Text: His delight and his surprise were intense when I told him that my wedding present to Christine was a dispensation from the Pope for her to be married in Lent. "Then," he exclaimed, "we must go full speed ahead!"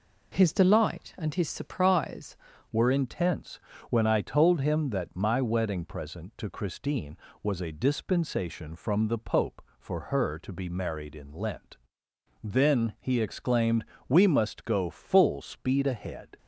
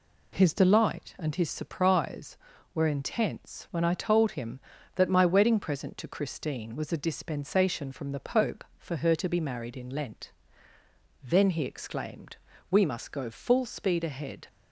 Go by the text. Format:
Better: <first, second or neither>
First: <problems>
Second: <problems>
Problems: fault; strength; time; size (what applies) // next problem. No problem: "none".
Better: second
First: changes voice at "were"; from 2.7 s on; 13.6 s long // pauses between "intense" and "when"; slight; at 3.5 s; 0.32 s long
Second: none